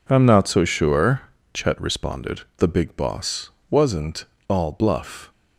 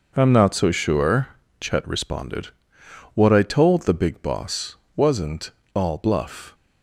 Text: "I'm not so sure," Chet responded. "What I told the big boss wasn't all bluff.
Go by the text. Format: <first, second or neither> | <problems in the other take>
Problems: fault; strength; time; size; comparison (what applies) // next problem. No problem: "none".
second | skips "What I told"; at 2.5 s // pauses between "boss" and "wasn't"; slight; at 3.5 s; 0.20 s long; slight in the second // pauses between "wasn't" and "all"; slight; at 4.2 s; 0.24 s long; slight in the second